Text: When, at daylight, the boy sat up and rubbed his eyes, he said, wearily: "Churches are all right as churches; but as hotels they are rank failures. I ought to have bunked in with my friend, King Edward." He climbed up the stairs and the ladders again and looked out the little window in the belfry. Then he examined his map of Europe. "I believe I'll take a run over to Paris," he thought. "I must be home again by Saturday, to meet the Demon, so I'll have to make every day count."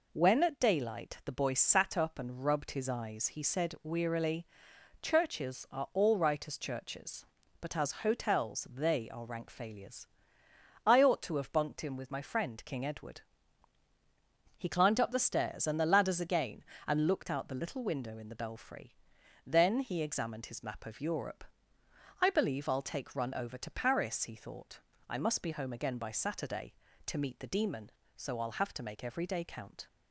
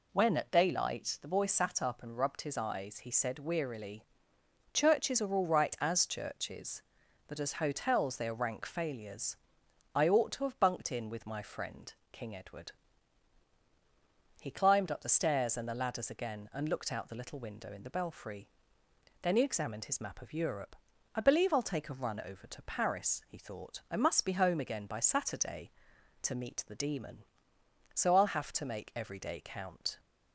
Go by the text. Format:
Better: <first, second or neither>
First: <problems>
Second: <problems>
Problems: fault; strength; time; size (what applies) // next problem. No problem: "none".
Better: second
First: skips "a"; at 23.1 s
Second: none